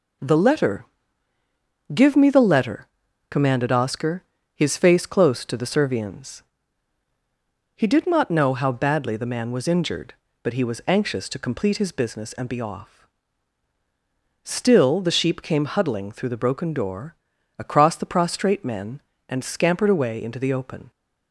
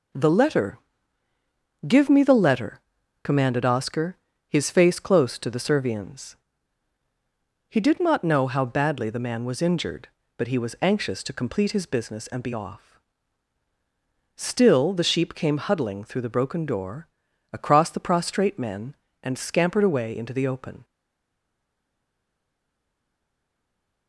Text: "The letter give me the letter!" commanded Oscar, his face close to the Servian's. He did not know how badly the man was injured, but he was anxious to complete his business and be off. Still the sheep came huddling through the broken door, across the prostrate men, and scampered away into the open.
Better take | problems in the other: first | pauses between "letter" and "give"; at 0.7 s; 1.0 s long; also in the first // stays silent after the last word; strong; from 20.8 s on; 3.2 s long

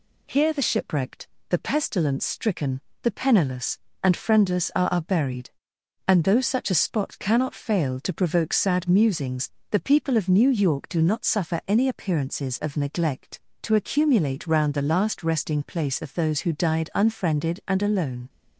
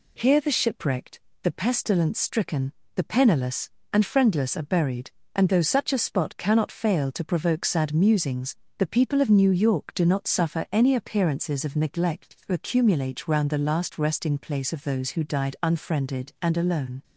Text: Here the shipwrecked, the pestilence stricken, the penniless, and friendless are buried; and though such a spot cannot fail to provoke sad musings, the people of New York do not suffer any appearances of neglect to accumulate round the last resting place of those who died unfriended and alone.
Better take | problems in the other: second | says "are" twice; at 4.9 s

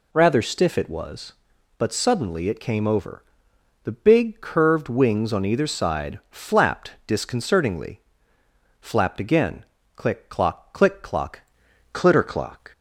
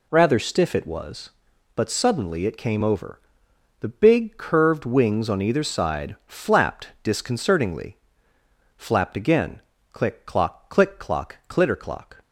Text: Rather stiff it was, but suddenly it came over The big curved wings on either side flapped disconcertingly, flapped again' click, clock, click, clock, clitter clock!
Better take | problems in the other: second | pauses between "over" and "The"; noticeable; at 3.2 s; 0.60 s long; noticeable in the second // pauses between "flapped" and "disconcertingly"; slight; at 6.9 s; 0.16 s long; slight in the second // pauses between "again" and "click"; slight; at 9.6 s; 0.30 s long; slight in the second // changes voice at "clitter"; from 11.9 s on; 0.8 s long

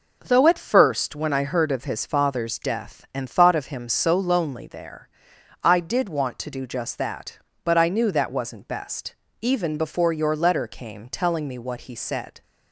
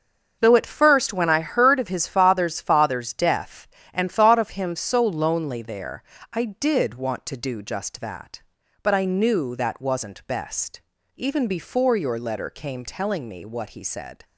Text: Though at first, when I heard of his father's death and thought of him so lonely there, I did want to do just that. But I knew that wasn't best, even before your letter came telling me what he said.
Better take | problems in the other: first | starts louder than the rest; until 1.4 s; 6.5 dB // says "father's" twice; at 2.6 s

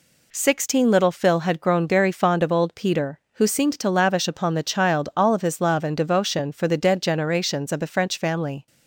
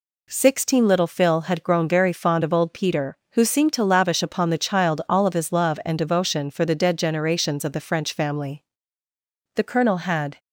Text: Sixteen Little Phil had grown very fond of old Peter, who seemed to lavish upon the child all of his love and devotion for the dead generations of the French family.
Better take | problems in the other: first | goes on to say "The colonel had"; noticeable; from 9.5 s on; 0.84 s long

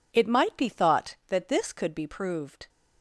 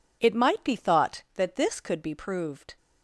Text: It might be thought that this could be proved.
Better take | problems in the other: neither | none

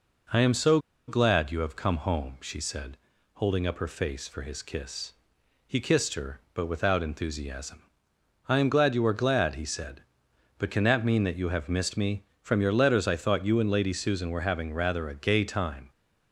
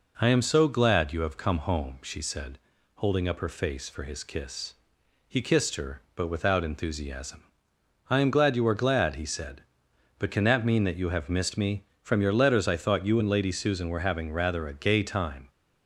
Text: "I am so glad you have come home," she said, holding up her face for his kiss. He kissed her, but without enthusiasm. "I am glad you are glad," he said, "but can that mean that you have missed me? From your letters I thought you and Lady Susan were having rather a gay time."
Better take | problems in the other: second | pauses between "so" and "glad"; slight; at 0.7 s; 0.29 s long

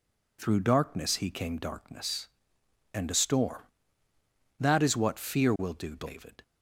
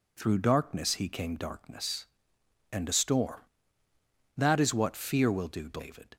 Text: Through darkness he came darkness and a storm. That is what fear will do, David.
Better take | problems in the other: neither | none

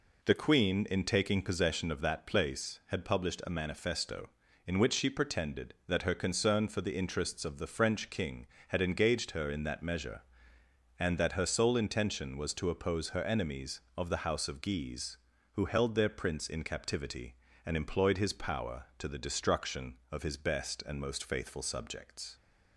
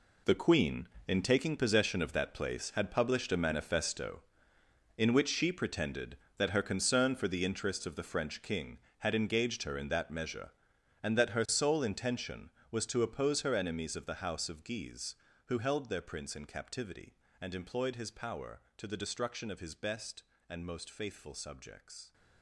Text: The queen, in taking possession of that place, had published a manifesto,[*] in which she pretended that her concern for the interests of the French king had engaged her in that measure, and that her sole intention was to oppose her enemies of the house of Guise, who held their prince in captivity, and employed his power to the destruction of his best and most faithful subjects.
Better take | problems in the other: first | gets quieter; strong; throughout; 10.5 dB

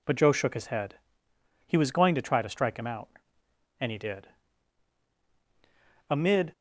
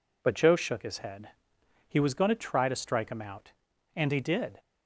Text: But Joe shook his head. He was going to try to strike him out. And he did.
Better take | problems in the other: second | goes on to say "Amid"; slight; from 6.0 s on; 0.42 s long

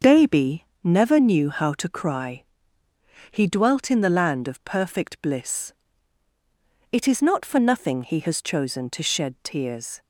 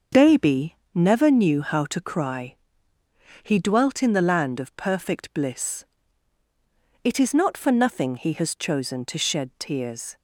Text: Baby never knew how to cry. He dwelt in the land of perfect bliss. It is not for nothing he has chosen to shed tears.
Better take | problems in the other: neither | starts louder than the rest; the same in both // pauses between "Baby" and "never"; slight; the same in both

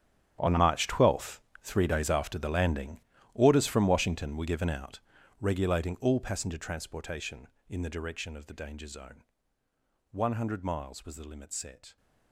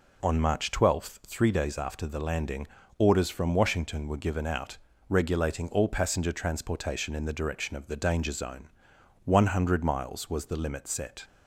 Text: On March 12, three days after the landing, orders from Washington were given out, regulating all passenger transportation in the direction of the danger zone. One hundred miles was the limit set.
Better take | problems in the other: second | gets quieter; strong; throughout; 17 dB

